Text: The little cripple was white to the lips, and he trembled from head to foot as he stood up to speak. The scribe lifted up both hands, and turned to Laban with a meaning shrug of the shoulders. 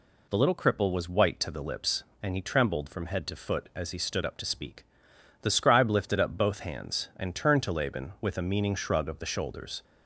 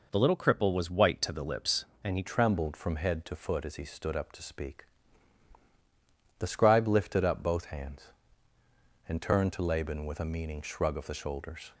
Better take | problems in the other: first | changes voice at "trembled"; from 2.2 s on; 9.5 s long

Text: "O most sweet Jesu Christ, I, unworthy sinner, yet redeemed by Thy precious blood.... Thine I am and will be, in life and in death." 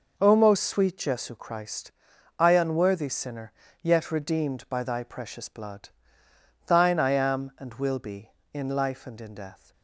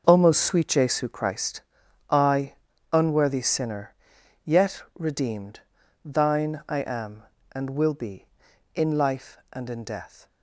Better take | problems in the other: first | starts louder than the rest; noticeable; until 1.0 s; 6 dB // skips "by Thy precious blood"; at 5.8 s

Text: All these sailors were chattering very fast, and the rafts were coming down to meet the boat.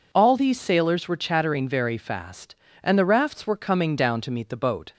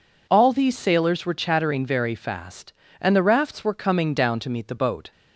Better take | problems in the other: neither | none

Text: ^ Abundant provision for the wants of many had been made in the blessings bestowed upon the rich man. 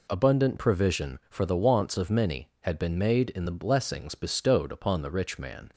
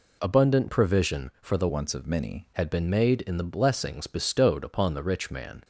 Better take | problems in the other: first | changes voice from "wants" to "many"; from 1.6 to 2.4 s; 0.8 s long

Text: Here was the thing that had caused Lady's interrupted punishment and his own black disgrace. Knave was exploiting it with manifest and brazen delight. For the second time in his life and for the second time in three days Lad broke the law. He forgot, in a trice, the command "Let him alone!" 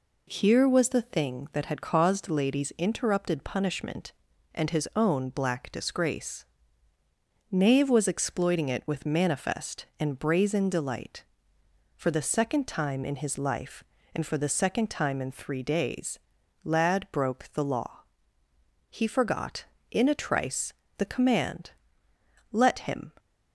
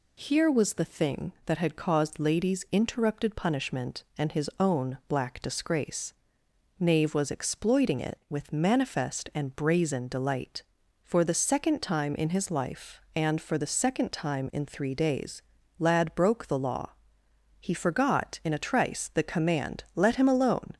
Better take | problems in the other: second | pauses between "days" and "Lad"; noticeable; at 16.1 s; 0.46 s long; also in the second // pauses between "command" and "Let"; noticeable; at 21.7 s; 0.80 s long // stops before "alone"; at 23.1 s

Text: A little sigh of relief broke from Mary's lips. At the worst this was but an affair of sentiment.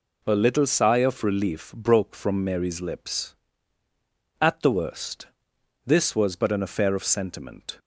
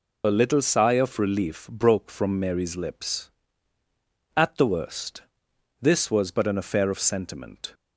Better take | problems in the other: first | loses the start of "A"; at 0.2 s; 50 ms // pauses between "worst" and "this"; noticeable; at 5.2 s; 0.58 s long; noticeable in the first

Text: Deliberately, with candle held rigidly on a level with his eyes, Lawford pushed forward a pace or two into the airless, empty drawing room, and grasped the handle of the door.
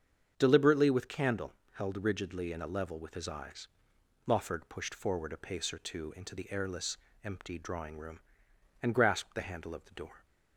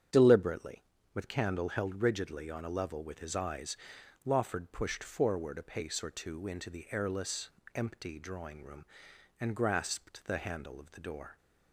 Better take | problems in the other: second | starts louder than the rest; strong; until 1.3 s; 7.5 dB; strong in the second // pauses between "candle" and "held"; slight; at 1.5 s; 0.20 s long // says "in" for "on"; at 2.5 s

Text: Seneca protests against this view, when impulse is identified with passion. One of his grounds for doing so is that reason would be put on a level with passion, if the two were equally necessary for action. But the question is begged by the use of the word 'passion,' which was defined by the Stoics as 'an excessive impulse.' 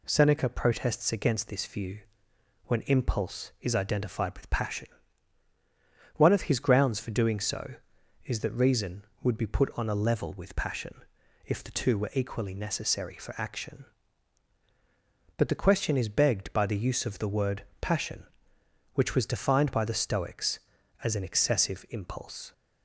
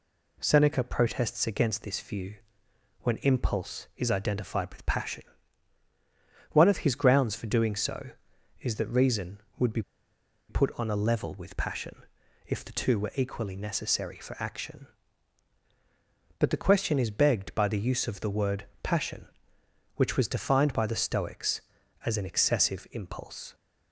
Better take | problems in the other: first | pauses between "be" and "put"; noticeable; at 9.8 s; 0.68 s long // pauses between "word" and "passion"; slight; at 18.6 s; 0.18 s long; slight in the first

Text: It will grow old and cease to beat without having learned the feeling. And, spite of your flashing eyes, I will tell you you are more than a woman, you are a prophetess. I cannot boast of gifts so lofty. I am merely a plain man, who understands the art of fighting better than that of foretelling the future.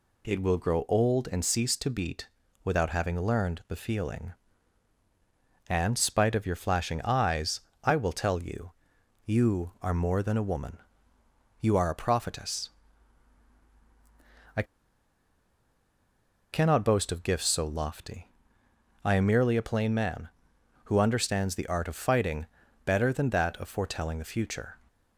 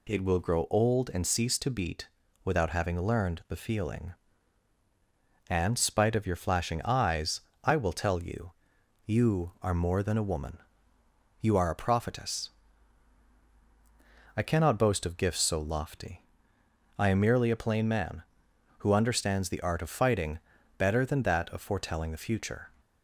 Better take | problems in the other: second | pauses between "beat" and "without"; at 2.2 s; 0.38 s long; also in the second // pauses between "you" and "you"; noticeable; at 8.7 s; 0.52 s long; noticeable in the second // pauses between "I" and "cannot"; strong; at 14.6 s; 1.8 s long // pauses between "fighting" and "better"; at 22.4 s; 0.40 s long; also in the second

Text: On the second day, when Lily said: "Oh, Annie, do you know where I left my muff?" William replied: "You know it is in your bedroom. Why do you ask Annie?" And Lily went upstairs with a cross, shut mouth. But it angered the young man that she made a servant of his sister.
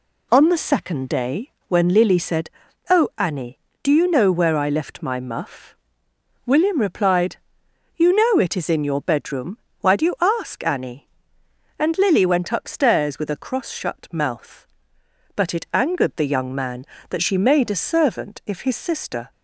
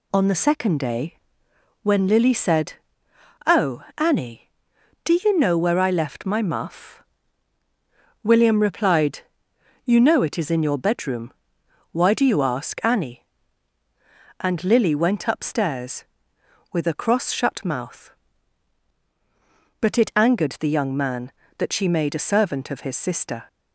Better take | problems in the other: second | says "if" for "of"; at 18.4 s

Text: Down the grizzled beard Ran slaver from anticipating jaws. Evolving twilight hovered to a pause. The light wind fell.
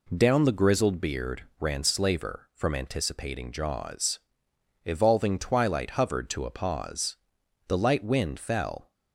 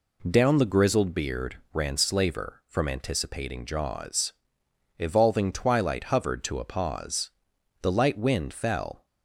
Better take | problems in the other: neither | pauses between "beard" and "Ran"; slight; the same in both

